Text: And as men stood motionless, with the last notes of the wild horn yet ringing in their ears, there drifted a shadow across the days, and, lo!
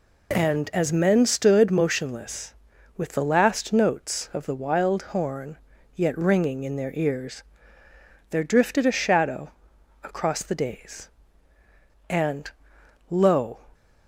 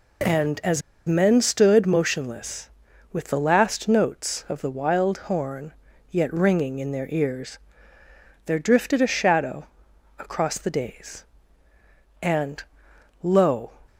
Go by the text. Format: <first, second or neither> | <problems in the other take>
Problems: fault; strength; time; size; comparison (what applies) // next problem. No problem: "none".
first | pauses between "as" and "men"; slight; at 0.8 s; 0.27 s long // pauses between "horn" and "yet"; slight; at 5.7 s; 0.36 s long; slight in the first // pauses between "shadow" and "across"; noticeable; at 9.6 s; 0.50 s long; noticeable in the first